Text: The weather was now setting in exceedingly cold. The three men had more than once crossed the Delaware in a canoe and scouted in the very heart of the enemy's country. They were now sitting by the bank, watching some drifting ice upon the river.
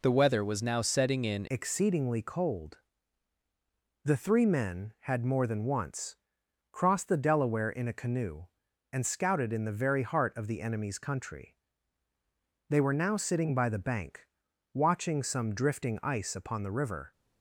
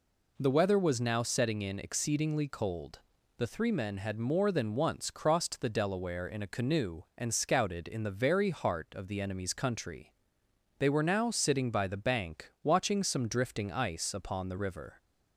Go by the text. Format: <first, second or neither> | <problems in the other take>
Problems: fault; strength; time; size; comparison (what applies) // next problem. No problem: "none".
second | changes voice at "exceedingly"; from 1.4 s on; 15.7 s long // pauses between "once" and "crossed"; noticeable; at 6.1 s; 0.56 s long